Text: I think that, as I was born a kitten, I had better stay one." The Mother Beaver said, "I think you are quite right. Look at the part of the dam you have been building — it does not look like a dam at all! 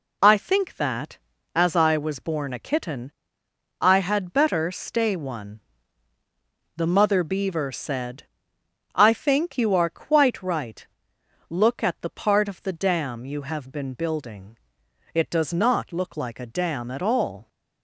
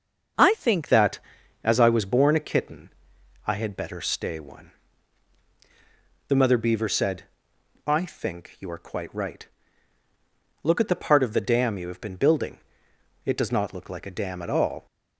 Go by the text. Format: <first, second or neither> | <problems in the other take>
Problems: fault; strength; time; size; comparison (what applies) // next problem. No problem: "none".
first | starts louder than the rest; until 1.8 s; 6.5 dB // changes voice at "that"; from 0.8 s on; 14.0 s long